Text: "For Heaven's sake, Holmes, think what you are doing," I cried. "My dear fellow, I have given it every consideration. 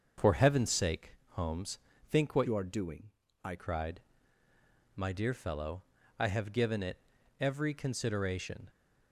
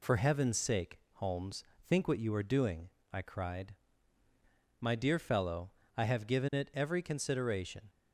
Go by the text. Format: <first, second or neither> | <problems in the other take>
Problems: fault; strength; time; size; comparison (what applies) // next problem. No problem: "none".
second | starts louder than the rest; until 1.3 s; 6.5 dB // changes voice from "you" to "I"; from 2.4 to 3.5 s; 1.1 s long // pauses between "it" and "every"; at 6.9 s; 0.40 s long